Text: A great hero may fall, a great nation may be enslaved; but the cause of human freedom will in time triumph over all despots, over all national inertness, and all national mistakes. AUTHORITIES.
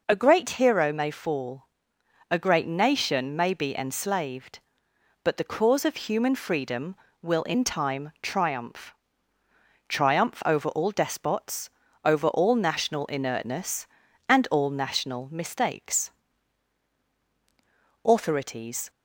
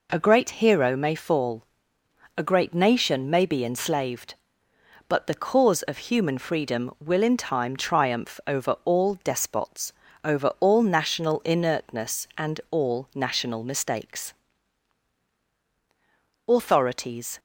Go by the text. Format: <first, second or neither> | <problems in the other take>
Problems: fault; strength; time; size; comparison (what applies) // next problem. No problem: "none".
second | says "triumph" twice; at 9.8 s